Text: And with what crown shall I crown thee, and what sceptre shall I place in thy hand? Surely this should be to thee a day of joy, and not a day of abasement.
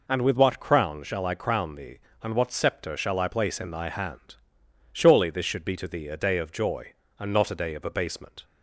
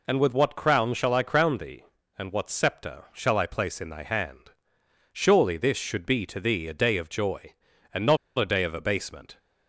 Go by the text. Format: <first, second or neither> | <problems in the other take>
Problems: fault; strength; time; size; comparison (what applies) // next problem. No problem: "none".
first | pauses between "not" and "a"; slight; at 8.1 s; 0.20 s long